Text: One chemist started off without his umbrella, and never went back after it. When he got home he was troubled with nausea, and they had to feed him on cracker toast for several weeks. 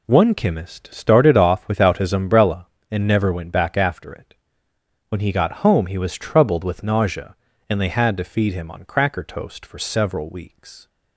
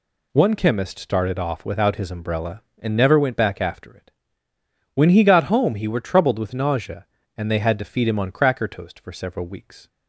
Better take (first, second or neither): first